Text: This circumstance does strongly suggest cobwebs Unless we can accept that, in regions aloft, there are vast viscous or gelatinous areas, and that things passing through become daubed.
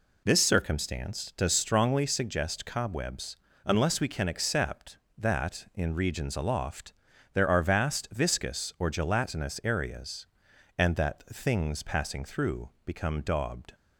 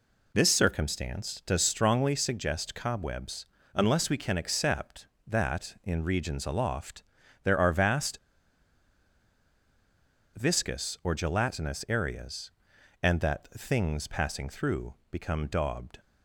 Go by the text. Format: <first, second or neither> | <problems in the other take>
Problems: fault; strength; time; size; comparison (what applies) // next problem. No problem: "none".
first | pauses between "cobwebs" and "Unless"; slight; at 3.4 s; 0.30 s long; slight in the first // pauses between "vast" and "viscous"; strong; at 8.1 s; 2.1 s long // pauses between "through" and "become"; slight; at 14.9 s; 0.16 s long